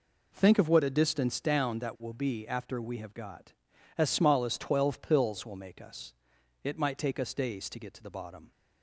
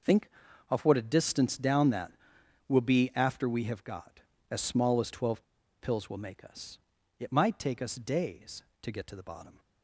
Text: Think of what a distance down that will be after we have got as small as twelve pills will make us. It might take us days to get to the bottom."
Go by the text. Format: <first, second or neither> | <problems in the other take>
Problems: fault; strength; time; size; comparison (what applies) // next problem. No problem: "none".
first | pauses between "twelve" and "pills"; at 5.4 s; 0.38 s long